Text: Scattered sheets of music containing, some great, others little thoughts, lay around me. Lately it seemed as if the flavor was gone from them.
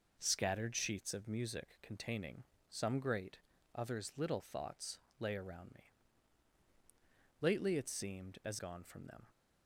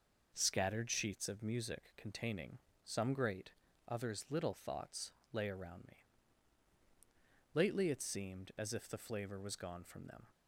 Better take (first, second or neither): second